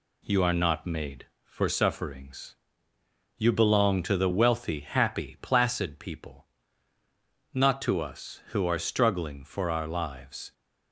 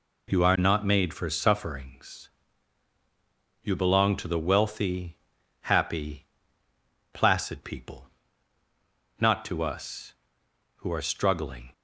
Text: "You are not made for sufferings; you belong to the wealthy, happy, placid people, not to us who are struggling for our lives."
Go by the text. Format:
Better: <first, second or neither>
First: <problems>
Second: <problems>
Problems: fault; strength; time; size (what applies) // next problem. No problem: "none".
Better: first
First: none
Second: stops before "for our lives"; at 11.7 s